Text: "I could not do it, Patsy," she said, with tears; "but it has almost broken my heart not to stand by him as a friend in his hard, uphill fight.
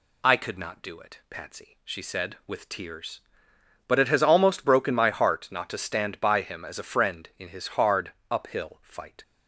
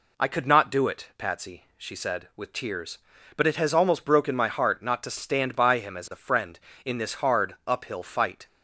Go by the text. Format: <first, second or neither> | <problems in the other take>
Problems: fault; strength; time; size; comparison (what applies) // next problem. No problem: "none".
first | says "this" for "his"; at 6.9 s